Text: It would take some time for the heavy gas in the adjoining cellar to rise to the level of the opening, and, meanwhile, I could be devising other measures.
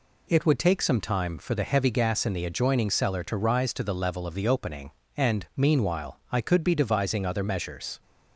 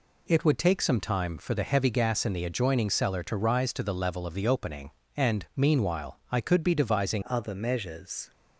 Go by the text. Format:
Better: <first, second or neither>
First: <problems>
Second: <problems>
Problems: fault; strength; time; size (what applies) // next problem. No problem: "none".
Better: first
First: none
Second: changes voice at "other"; from 7.2 s on; 1.1 s long